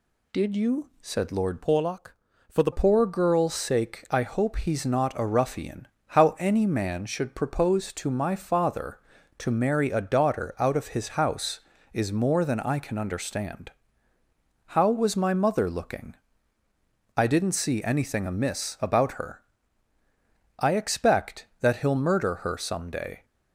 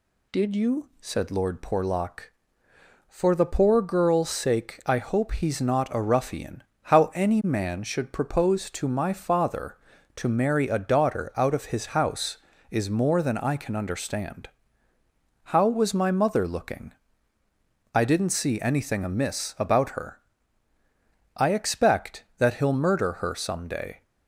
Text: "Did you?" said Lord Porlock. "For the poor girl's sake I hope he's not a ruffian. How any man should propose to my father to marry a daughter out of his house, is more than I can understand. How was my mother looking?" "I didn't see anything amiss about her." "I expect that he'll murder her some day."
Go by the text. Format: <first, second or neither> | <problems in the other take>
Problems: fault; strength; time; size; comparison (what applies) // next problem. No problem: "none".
second | changes voice from "Porlock" to "the"; from 1.6 to 2.7 s; 1.1 s long